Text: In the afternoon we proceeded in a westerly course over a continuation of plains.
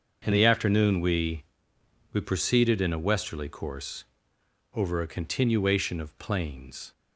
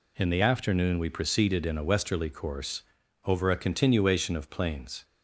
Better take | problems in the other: second | starts louder than the rest; until 1.2 s; 6.5 dB // says "we" twice; at 2.1 s // pauses between "course" and "over"; noticeable; at 4.0 s; 0.68 s long; also in the second

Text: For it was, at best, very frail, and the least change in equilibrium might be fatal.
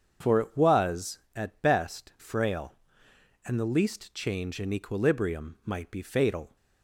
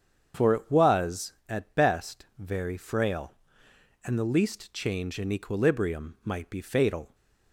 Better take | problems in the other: second | starts louder than the rest; strong; until 1.4 s; 7 dB; strong in the second // skips "very"; at 2.1 s

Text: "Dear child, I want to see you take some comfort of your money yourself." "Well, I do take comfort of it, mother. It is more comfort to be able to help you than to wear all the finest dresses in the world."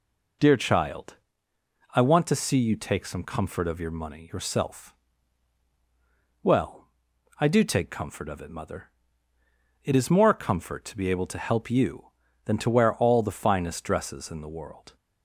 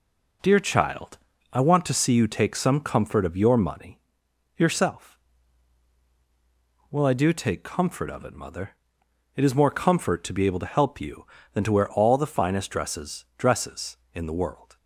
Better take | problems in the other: first | pauses between "money" and "yourself"; noticeable; at 3.9 s; 0.56 s long // says "dresses" twice; at 13.3 s

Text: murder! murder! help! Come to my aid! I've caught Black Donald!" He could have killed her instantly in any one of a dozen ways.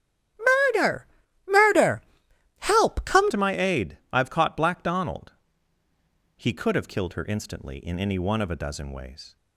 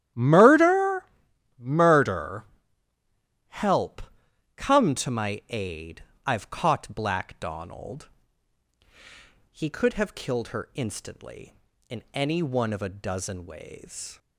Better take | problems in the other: second | starts louder than the rest; strong; until 1.8 s; 11.5 dB; strong in the second // changes voice at "to"; from 3.3 s on; 6.0 s long

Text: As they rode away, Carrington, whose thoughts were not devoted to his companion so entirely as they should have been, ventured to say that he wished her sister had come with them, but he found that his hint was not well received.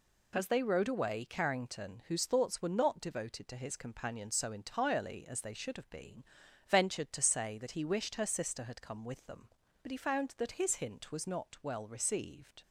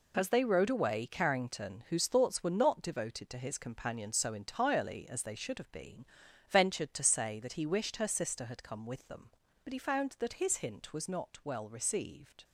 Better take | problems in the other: first | gets quieter; strong; throughout; 9 dB

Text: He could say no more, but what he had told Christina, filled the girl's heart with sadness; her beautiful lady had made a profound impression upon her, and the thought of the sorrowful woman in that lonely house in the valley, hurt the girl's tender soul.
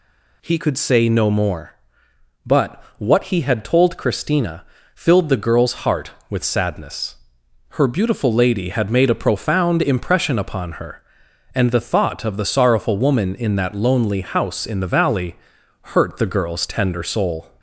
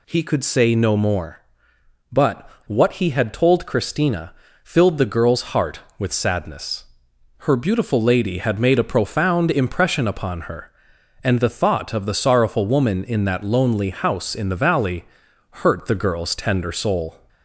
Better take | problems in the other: neither | pauses between "but" and "what"; slight; the same in both

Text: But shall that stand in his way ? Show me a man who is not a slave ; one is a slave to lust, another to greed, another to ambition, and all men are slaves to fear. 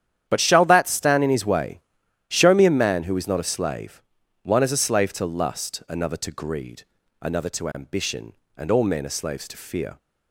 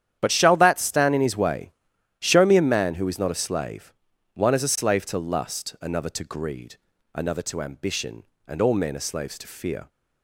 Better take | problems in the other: neither | starts louder than the rest; strong; the same in both

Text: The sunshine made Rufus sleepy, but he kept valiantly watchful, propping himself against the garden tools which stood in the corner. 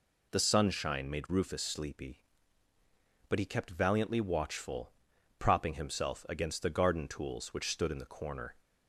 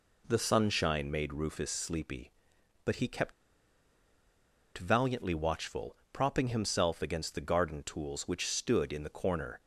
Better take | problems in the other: first | pauses between "kept" and "valiantly"; strong; at 3.3 s; 1.4 s long

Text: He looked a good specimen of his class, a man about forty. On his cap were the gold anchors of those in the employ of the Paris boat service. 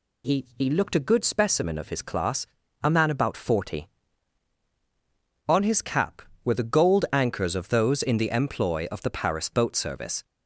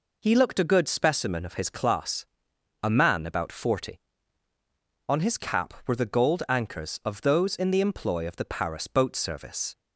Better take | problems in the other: second | says "He" twice; at 0.5 s

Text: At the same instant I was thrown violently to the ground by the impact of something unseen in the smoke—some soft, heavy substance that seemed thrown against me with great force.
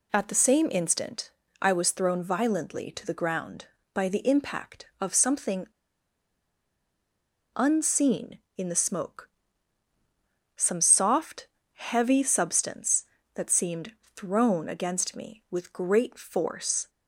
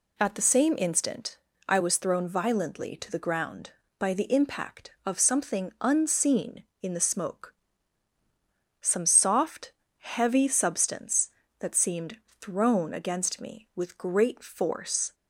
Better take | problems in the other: second | pauses between "instant" and "I"; slight; at 1.2 s; 0.32 s long; slight in the second // pauses between "something" and "unseen"; strong; at 5.6 s; 1.8 s long // pauses between "seemed" and "thrown"; slight; at 13.9 s; 0.22 s long; slight in the second

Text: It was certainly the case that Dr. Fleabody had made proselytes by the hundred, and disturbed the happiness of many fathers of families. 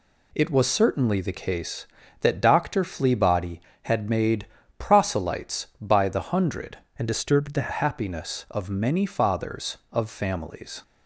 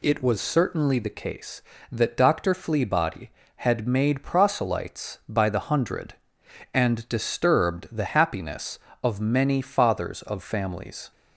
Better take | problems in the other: second | pauses between "made" and "proselytes"; slight; at 4.4 s; 0.32 s long // changes voice from "and" to "the"; from 6.9 to 7.7 s; 0.8 s long

